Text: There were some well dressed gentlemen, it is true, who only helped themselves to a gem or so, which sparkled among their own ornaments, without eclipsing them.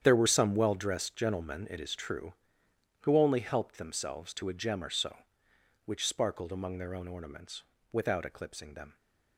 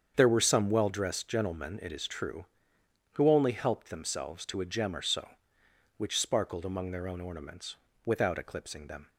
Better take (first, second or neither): second